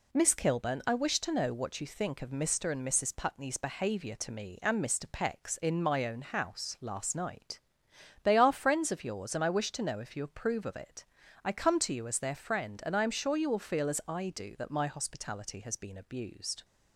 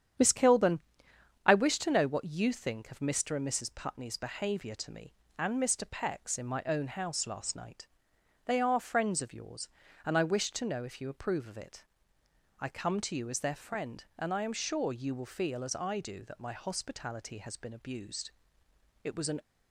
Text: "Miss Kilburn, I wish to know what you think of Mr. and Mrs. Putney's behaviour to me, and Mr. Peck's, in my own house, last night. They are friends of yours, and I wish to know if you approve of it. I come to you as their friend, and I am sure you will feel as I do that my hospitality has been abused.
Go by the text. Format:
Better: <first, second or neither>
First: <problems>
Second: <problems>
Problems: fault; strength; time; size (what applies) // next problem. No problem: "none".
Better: first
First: none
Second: starts louder than the rest; strong; until 1.8 s; 9 dB // goes on to say "It was an"; slight; from 19.0 s on; 0.36 s long